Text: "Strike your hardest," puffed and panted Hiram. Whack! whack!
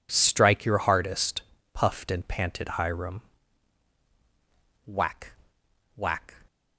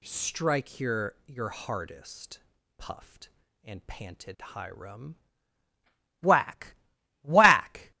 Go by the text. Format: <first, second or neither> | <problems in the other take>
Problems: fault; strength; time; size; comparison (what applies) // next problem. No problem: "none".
first | says "your" twice; at 1.2 s